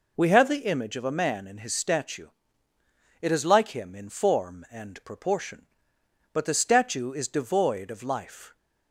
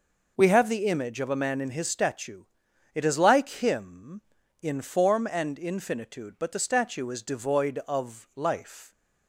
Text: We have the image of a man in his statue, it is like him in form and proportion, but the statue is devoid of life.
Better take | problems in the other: first | says "infinitude" for "proportion"; at 5.5 s

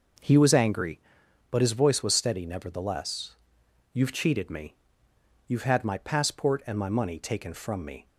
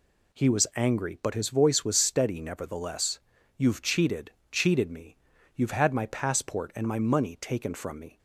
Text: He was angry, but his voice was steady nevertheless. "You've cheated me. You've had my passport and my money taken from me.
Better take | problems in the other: first | says "cheated" twice; at 4.4 s

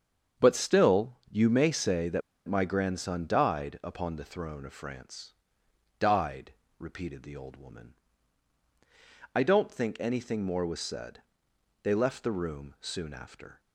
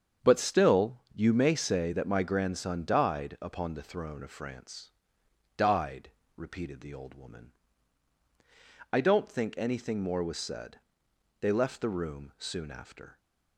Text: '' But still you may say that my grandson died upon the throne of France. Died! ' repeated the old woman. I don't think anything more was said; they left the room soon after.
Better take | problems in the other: second | starts louder than the rest; strong; until 1.5 s; 7.5 dB; strong in the second // pauses between "that" and "my"; slight; at 2.2 s; 0.26 s long

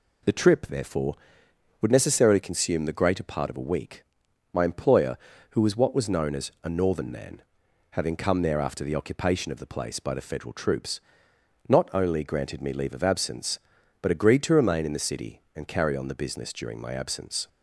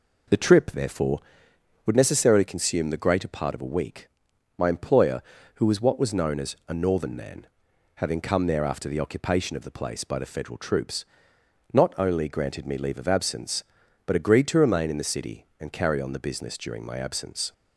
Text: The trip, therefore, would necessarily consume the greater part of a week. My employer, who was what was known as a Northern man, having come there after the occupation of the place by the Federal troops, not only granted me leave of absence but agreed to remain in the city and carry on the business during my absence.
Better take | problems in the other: first | starts louder than the rest; until 1.2 s; 4 dB

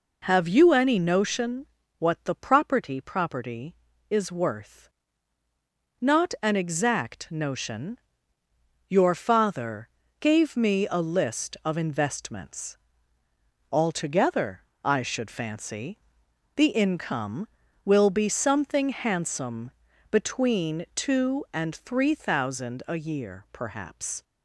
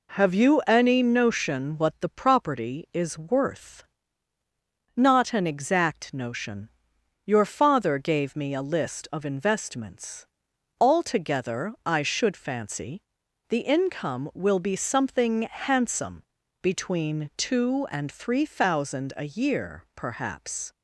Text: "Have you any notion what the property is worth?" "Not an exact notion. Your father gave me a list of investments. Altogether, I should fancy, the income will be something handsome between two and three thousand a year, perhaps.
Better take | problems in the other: second | pauses between "notion" and "what"; slight; at 1.6 s; 0.34 s long // says "property" twice; at 3.0 s // pauses between "father" and "gave"; slight; at 9.8 s; 0.32 s long // pauses between "handsome" and "between"; at 19.7 s; 0.38 s long; slight in the second

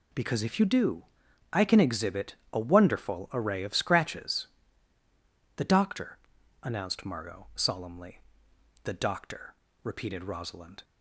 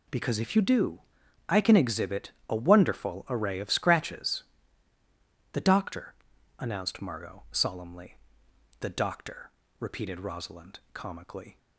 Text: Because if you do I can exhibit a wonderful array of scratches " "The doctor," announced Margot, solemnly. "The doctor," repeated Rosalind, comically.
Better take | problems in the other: second | pauses between "do" and "I"; noticeable; at 1.0 s; 0.50 s long; noticeable in the second // pauses between "exhibit" and "a"; slight; at 2.3 s; 0.18 s long; slight in the second // stops before "comically"; at 10.8 s

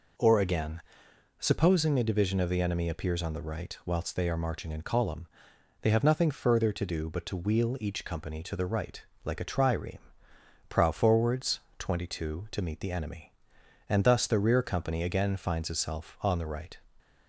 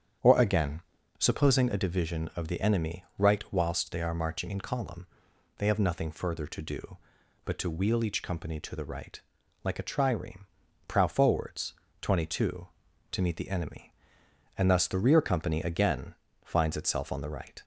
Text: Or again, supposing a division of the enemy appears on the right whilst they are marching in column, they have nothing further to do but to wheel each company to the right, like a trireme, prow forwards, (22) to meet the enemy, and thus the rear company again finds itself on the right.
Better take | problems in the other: first | starts louder than the rest; strong; until 1.5 s; 8.5 dB // skips "appears on the"; at 3.1 s // pauses between "again" and "finds"; slight; at 16.1 s; 0.30 s long

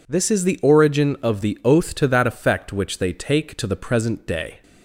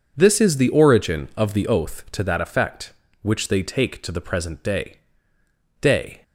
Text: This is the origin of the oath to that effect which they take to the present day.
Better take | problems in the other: first | says "day" twice; at 5.8 s

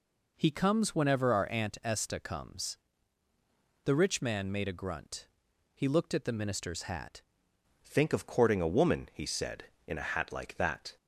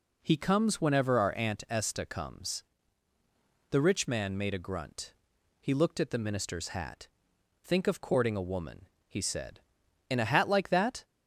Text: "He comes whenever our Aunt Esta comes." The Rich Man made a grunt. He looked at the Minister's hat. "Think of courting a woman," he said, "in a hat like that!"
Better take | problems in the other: second | changes voice at "Think"; from 7.8 s on; 3.1 s long

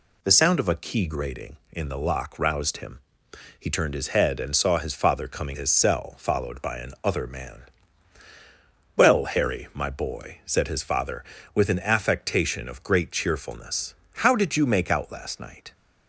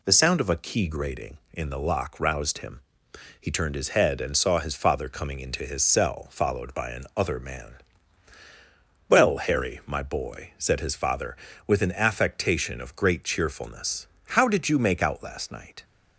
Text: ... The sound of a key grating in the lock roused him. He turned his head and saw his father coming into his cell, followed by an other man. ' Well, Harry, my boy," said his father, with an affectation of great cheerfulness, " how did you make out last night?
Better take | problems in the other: second | skips "into"; at 5.5 s

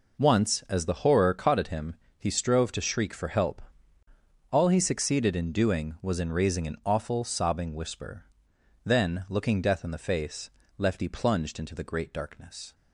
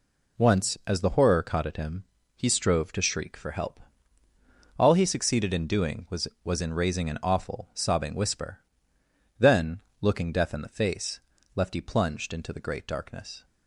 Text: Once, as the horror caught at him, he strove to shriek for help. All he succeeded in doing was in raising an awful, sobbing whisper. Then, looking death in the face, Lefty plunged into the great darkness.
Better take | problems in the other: first | says "was" twice; at 6.4 s

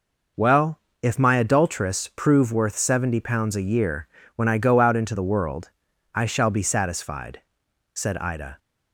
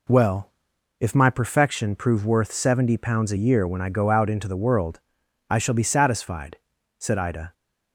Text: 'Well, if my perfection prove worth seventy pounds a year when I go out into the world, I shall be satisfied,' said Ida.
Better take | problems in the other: second | says "adulteress" for "perfection"; at 1.3 s // pauses between "year" and "when"; slight; at 4.0 s; 0.28 s long

